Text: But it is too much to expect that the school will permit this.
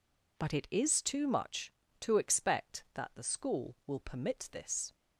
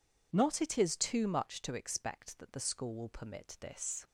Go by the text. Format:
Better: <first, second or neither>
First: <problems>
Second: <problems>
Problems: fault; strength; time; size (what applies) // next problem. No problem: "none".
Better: first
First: none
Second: says "Not" for "But"; at 0.3 s